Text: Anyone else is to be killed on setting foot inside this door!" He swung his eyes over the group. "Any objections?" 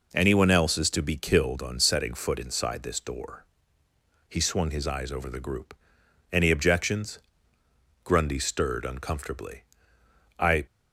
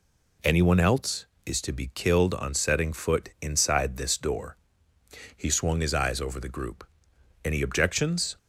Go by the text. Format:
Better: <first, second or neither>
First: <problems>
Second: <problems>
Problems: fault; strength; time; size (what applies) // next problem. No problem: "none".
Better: second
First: goes on to say "Grundy stirred uncomfortably I"; strong; from 8.0 s on; 2.6 s long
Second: none